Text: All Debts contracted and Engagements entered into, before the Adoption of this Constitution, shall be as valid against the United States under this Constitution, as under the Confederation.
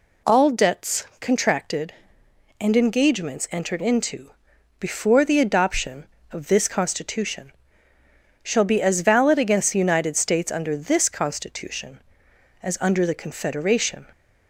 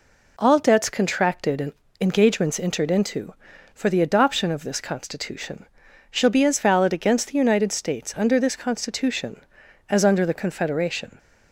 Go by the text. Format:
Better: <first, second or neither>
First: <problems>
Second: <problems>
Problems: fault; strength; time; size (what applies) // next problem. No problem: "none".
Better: first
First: none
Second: pauses between "and" and "Engagements"; slight; at 1.7 s; 0.28 s long // says "for" for "before"; at 3.7 s